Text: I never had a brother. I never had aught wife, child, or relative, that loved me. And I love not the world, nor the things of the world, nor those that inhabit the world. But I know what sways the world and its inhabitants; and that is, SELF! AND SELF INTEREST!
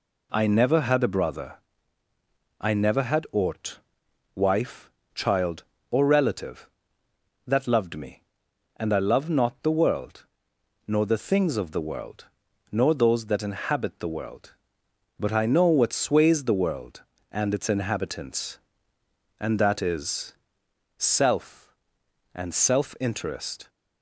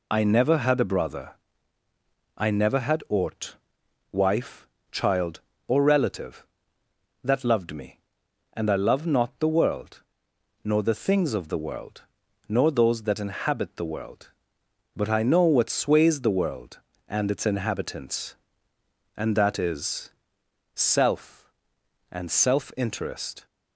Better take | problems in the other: first | loses the start of "I"; at 0.1 s; 35 ms // pauses between "aught" and "wife"; noticeable; at 3.5 s; 0.52 s long; noticeable in the first

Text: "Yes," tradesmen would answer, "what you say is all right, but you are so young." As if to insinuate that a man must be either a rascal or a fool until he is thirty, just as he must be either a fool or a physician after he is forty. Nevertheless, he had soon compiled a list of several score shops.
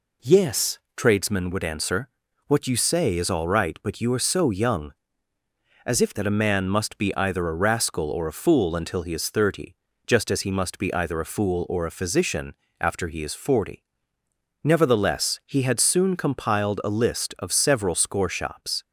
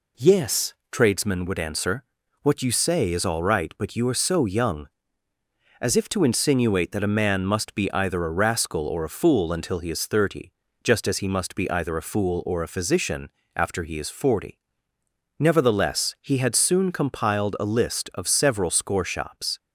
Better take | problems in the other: second | skips "to insinuate"; at 6.1 s // pauses between "physician" and "after"; slight; at 12.5 s; 0.26 s long; slight in the second

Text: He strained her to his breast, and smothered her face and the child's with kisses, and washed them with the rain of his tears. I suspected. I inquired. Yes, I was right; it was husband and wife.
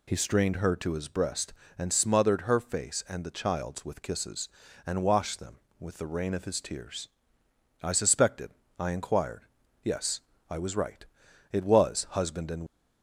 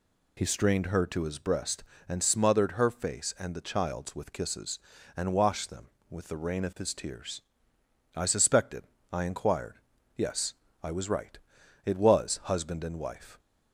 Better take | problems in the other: second | stops before "wife"; at 12.6 s

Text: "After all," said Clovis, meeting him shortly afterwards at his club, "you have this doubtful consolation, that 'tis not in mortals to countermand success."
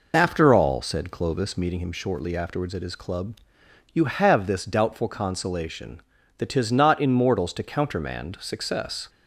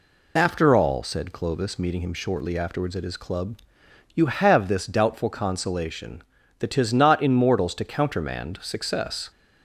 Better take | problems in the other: second | starts louder than the rest; noticeable; until 1.8 s; 5 dB

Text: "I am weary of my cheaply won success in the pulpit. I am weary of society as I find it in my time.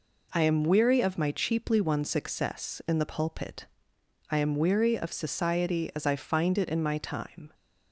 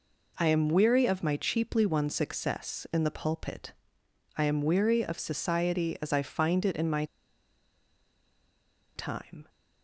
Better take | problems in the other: first | pauses between "my" and "time"; strong; at 7.0 s; 1.9 s long

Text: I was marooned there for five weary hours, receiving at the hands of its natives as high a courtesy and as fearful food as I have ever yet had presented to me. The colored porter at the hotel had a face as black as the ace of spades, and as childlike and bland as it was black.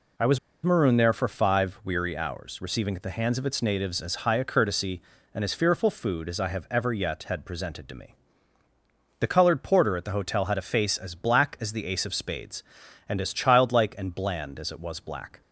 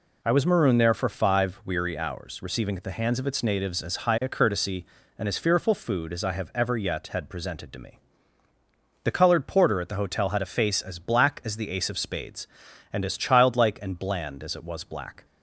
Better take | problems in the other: second | pauses between "was" and "marooned"; slight; at 0.3 s; 0.26 s long

